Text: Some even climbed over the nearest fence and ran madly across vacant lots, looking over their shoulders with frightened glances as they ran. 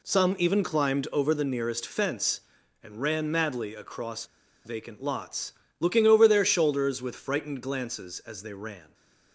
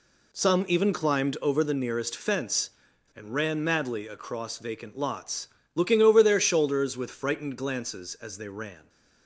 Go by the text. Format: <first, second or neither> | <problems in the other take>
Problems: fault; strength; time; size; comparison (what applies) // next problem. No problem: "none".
second | pauses between "across" and "vacant"; at 4.2 s; 0.38 s long